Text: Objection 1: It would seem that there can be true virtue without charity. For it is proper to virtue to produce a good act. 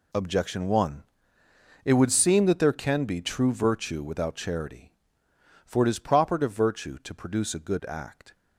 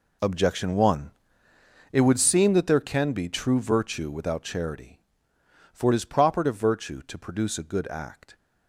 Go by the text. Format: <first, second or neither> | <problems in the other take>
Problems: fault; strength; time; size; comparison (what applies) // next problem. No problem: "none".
first | starts louder than the rest; until 1.7 s; 3.5 dB